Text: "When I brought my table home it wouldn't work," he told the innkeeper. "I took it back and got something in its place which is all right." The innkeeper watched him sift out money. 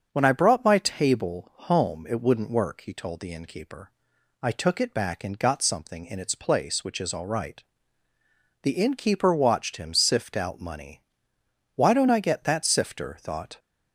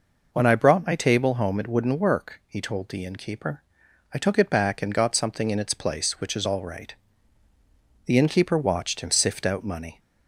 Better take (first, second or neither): second